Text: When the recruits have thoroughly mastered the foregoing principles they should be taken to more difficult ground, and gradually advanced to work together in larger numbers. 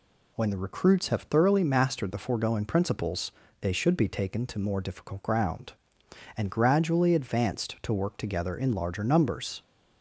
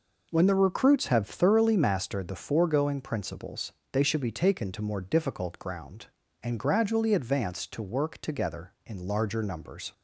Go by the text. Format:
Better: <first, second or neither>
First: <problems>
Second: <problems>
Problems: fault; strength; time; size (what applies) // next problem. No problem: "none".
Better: neither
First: pauses between "principles" and "they"; slight; at 3.2 s; 0.30 s long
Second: pauses between "principles" and "they"; slight; at 3.7 s; 0.20 s long